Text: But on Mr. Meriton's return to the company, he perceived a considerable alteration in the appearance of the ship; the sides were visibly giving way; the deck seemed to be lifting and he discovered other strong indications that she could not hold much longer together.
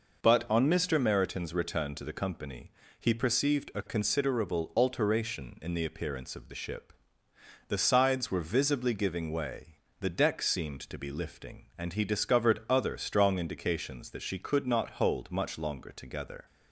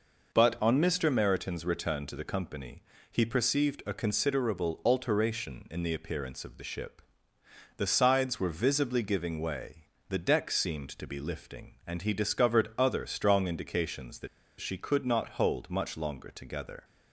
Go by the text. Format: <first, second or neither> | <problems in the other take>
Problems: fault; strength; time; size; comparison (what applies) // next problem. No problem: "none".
first | pauses between "that" and "she"; slight; at 14.2 s; 0.32 s long